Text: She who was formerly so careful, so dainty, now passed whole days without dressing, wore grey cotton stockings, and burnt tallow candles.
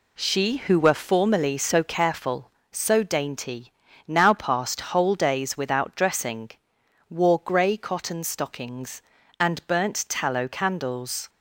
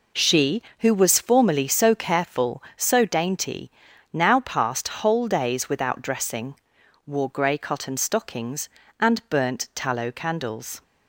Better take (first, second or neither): second